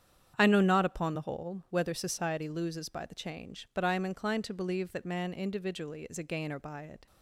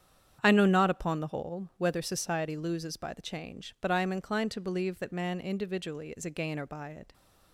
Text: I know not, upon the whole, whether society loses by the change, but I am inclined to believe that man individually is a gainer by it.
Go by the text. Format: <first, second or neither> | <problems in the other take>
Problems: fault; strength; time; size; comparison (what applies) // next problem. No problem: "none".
neither | starts louder than the rest; strong; the same in both